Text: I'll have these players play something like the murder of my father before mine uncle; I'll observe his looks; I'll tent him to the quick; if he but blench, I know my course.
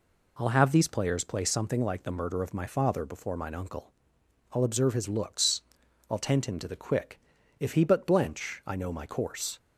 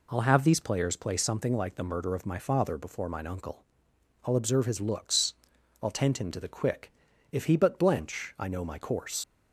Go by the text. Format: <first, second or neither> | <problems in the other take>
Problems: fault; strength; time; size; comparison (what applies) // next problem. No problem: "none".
first | leaves "course" unfinished; at 9.2 s; 55 ms